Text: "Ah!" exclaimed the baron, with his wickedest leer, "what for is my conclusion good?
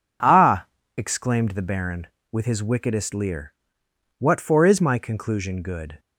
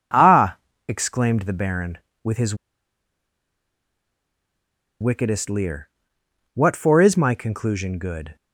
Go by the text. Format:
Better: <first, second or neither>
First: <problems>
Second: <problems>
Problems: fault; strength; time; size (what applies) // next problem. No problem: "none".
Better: first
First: none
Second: pauses between "his" and "wickedest"; strong; at 2.5 s; 2.4 s long